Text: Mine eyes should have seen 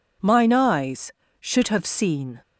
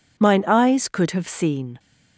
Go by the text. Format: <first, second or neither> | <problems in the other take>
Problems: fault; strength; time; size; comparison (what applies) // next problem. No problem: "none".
first | says "could" for "should"; at 0.8 s